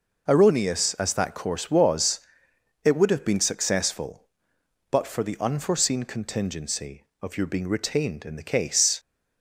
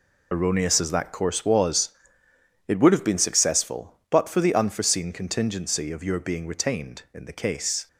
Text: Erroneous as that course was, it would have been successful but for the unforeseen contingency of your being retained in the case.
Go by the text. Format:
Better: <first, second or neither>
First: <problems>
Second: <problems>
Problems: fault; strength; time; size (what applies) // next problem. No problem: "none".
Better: first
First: none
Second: loses the start of "Erroneous"; at 0.3 s; 40 ms